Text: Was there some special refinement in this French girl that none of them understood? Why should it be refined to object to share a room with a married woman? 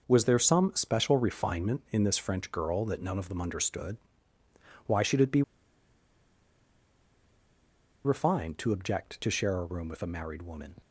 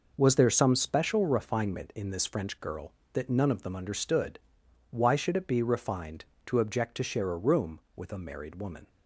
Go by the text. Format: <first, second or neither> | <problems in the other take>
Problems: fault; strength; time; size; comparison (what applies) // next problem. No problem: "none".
second | pauses between "be" and "refined"; strong; at 5.4 s; 2.6 s long